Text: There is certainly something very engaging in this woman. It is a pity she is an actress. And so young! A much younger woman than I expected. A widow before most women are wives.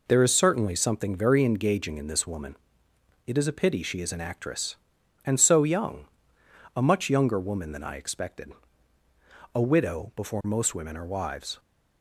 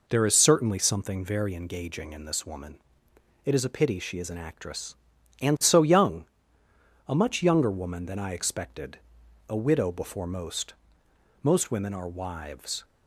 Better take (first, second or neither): first